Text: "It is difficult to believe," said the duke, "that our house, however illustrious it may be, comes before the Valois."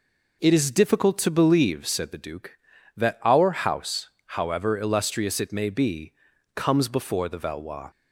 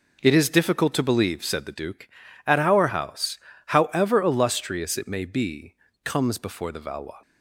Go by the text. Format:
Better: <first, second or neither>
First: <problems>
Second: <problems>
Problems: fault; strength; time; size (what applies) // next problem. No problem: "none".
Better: first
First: none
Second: says "at" for "that"; at 2.4 s